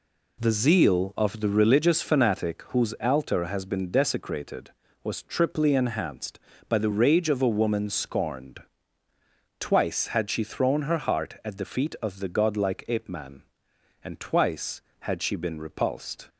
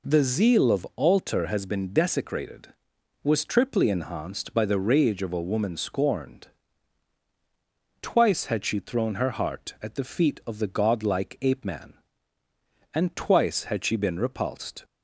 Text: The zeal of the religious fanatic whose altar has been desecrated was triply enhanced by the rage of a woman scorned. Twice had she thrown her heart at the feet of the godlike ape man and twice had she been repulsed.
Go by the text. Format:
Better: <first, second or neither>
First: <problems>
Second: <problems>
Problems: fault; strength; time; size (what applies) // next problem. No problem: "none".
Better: first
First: none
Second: skips "the religious fanatic whose"; at 0.9 s